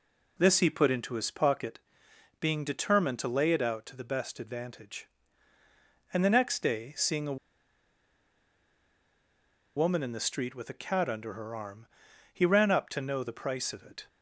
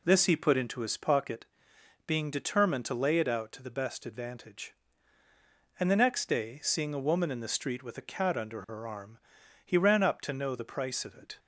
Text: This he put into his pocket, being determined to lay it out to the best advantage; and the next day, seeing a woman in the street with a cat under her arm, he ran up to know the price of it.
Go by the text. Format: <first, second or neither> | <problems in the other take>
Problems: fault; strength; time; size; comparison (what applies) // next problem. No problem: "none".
second | pauses between "a" and "woman"; strong; at 7.3 s; 2.4 s long